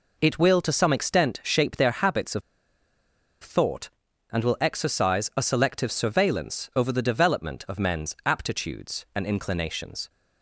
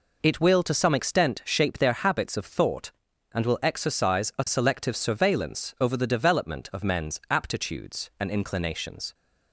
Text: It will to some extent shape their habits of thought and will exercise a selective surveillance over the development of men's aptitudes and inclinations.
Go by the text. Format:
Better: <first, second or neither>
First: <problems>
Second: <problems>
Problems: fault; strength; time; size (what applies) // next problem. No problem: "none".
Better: second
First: pauses between "of" and "thought"; at 2.4 s; 1.0 s long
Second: none